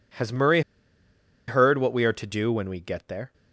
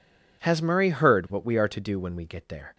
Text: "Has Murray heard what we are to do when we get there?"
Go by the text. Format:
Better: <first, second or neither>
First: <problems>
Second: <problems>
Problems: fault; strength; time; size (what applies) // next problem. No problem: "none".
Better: second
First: pauses between "Murray" and "heard"; noticeable; at 0.6 s; 0.87 s long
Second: none